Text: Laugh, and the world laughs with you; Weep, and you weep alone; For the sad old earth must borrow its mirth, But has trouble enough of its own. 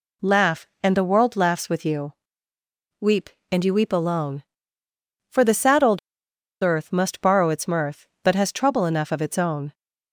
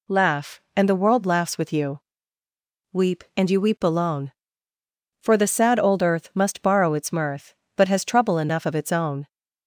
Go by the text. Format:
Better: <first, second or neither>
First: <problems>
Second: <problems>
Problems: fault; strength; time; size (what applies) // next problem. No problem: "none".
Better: second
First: pauses between "old" and "earth"; noticeable; at 5.9 s; 0.64 s long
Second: none